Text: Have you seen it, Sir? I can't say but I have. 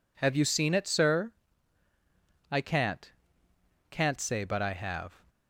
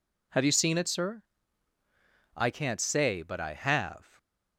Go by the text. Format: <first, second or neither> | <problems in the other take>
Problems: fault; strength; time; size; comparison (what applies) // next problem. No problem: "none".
second | says "can't" twice; at 3.8 s